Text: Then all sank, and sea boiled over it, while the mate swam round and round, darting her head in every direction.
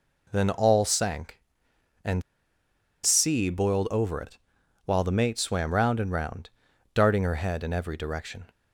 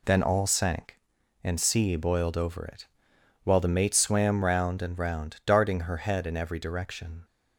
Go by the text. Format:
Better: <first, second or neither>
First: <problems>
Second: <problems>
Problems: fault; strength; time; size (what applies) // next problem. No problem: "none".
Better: second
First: pauses between "and" and "sea"; noticeable; at 2.2 s; 0.81 s long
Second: none